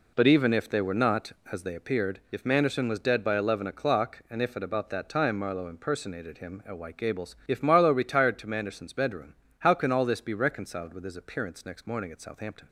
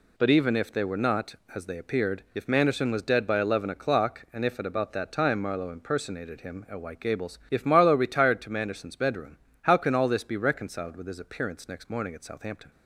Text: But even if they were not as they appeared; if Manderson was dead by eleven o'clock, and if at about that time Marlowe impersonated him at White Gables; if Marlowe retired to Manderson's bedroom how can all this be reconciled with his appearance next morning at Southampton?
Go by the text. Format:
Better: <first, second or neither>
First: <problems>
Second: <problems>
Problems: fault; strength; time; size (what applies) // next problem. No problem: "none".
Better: second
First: starts louder than the rest; slight; until 1.9 s; 3 dB // pauses between "bedroom" and "how"; slight; at 9.3 s; 0.26 s long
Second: pauses between "bedroom" and "how"; slight; at 9.3 s; 0.26 s long